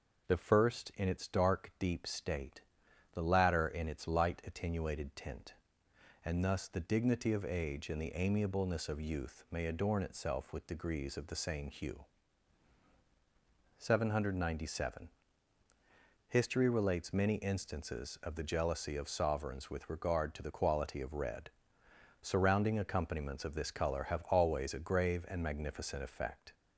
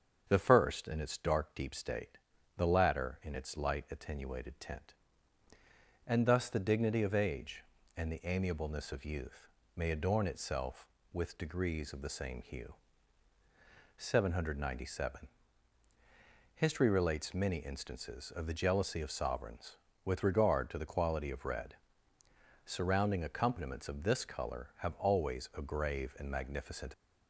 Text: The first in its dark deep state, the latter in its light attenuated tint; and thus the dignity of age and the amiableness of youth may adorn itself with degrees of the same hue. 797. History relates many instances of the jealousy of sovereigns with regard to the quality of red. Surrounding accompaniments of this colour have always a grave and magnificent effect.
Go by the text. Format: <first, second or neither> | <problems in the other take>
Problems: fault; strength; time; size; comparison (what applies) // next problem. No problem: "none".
first | starts louder than the rest; strong; until 1.2 s; 7 dB // pauses between "youth" and "may"; slight; at 9.4 s; 0.30 s long // stops before "effect"; at 26.9 s